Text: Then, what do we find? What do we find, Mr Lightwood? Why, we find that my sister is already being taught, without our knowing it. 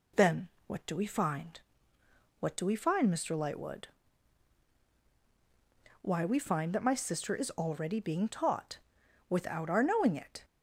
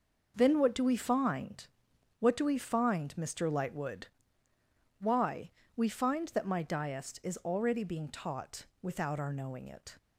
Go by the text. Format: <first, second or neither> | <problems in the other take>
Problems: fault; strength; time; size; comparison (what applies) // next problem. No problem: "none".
first | says "diest" for "sister"; at 6.6 s